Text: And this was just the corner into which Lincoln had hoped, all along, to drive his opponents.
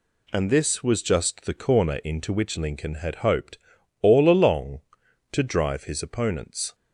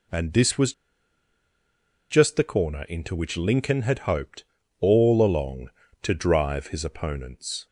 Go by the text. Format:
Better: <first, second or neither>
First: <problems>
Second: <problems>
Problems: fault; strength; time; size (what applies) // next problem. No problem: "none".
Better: first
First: none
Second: pauses between "was" and "just"; strong; at 0.7 s; 1.3 s long